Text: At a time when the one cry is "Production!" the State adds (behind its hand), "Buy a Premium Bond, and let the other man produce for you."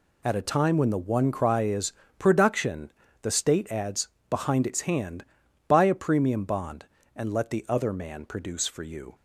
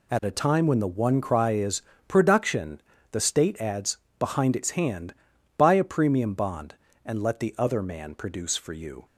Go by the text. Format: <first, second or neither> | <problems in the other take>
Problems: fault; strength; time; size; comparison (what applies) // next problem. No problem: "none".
neither | pauses between "is" and "Production"; slight; the same in both